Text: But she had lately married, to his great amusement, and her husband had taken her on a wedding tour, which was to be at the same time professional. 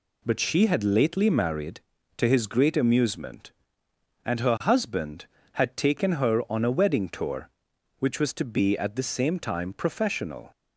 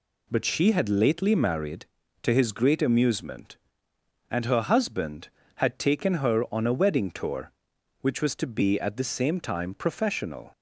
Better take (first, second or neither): neither